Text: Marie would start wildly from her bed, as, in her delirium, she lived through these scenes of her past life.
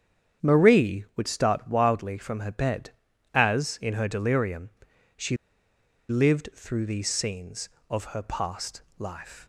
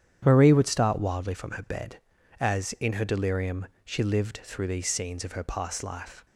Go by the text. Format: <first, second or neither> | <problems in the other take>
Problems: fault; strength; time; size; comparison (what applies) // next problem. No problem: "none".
second | starts louder than the rest; strong; until 1.5 s; 8.5 dB; strong in the second // pauses between "she" and "lived"; noticeable; at 5.3 s; 0.73 s long // pauses between "past" and "life"; slight; at 8.8 s; 0.16 s long